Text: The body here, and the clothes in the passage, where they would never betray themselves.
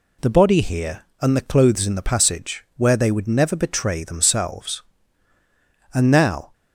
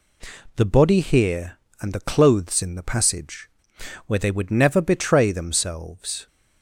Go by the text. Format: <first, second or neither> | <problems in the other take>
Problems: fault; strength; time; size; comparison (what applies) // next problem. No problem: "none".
second | goes on to say "And now"; from 5.9 s on; 0.60 s long